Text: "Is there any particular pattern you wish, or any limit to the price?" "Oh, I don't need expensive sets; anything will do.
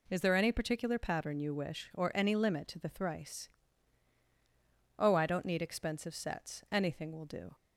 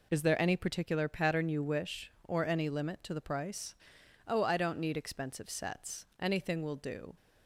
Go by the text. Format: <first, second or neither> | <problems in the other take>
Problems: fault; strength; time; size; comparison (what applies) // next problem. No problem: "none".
second | says "thrice" for "price"; at 2.8 s